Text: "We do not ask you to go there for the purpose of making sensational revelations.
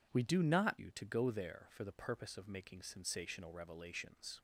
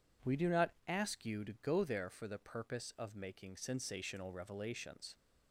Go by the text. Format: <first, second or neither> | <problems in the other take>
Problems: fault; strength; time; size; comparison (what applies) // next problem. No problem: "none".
second | skips "ask"; at 0.7 s